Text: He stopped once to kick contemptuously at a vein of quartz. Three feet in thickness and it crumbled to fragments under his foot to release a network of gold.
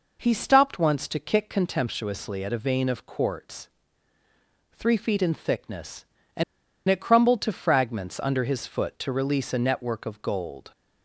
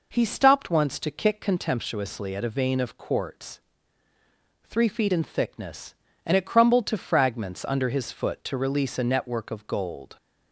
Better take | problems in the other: second | pauses between "and" and "it"; at 6.4 s; 0.45 s long

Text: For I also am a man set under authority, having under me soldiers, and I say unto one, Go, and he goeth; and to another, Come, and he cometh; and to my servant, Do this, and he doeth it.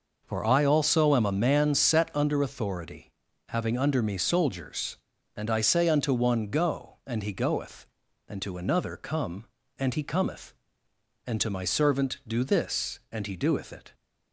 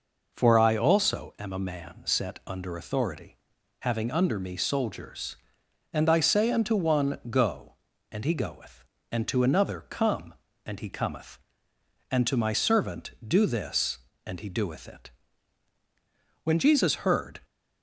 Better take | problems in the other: first | goes on to say "When Jesus heard"; noticeable; from 16.4 s on; 0.98 s long

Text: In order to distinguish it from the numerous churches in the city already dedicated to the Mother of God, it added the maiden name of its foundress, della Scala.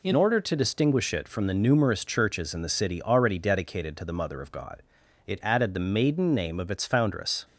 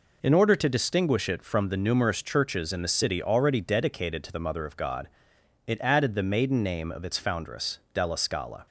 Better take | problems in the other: second | stops before "della Scala"; at 7.4 s

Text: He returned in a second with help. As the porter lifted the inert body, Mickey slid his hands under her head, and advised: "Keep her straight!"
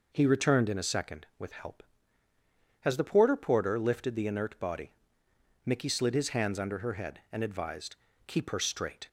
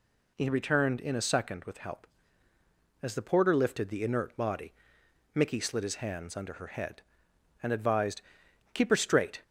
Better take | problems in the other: second | says "porter" twice; at 3.3 s

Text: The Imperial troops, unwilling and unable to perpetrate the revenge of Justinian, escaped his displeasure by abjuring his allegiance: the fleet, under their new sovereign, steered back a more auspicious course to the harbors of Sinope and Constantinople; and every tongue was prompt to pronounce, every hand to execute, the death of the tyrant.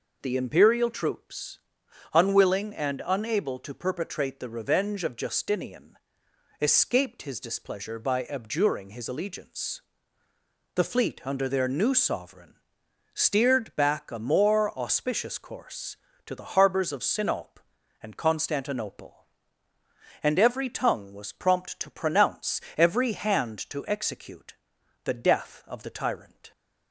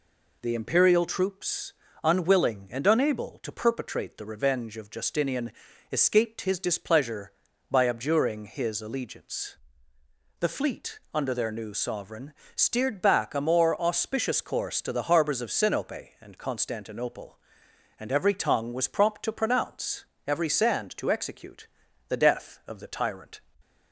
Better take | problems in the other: first | says "sand" for "hand"; at 20.4 s

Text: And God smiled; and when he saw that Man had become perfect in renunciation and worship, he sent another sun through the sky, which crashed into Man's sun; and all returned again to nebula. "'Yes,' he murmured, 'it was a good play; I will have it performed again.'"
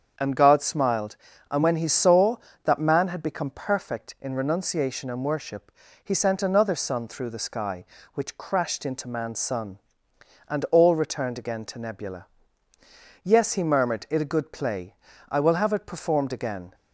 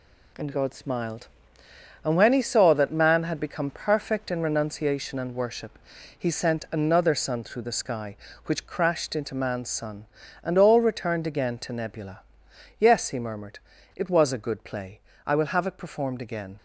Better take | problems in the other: second | starts louder than the rest; strong; until 1.5 s; 7.5 dB // skips "was"; at 14.2 s

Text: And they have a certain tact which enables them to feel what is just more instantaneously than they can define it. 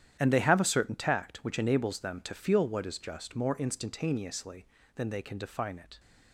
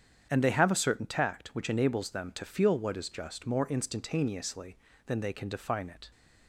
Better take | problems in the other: second | gets quieter; strong; throughout; 14 dB // starts louder than the rest; strong; until 1.2 s; 10.5 dB; strong in the second

